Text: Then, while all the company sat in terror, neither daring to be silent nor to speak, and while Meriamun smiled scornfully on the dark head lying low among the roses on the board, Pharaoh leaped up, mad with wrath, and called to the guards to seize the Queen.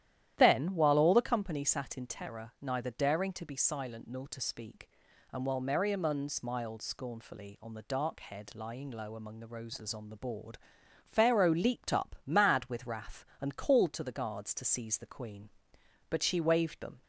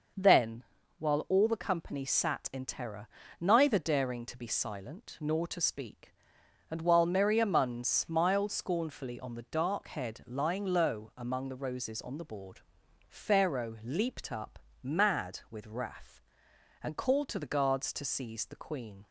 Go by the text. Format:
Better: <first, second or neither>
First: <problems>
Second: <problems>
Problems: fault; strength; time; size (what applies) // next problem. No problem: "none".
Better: second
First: starts louder than the rest; strong; until 1.3 s; 12 dB // goes on to say "But she waved them"; noticeable; from 16.0 s on; 0.92 s long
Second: none